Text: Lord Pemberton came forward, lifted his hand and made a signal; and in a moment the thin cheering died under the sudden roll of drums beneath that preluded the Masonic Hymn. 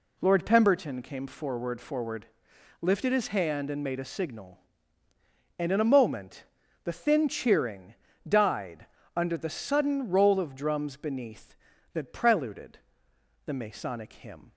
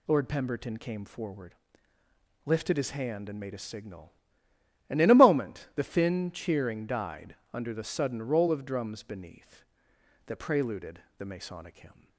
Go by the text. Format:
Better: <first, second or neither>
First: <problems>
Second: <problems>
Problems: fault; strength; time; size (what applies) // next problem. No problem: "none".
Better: second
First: says "forward" twice; at 1.7 s // pauses between "moment" and "the"; at 6.4 s; 0.40 s long // pauses between "cheering" and "died"; slight; at 7.9 s; 0.34 s long // pauses between "died" and "under"; slight; at 8.8 s; 0.28 s long // pauses between "preluded" and "the"; noticeable; at 12.7 s; 0.66 s long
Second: pauses between "died" and "under"; slight; at 7.3 s; 0.18 s long // pauses between "preluded" and "the"; slight; at 11.0 s; 0.18 s long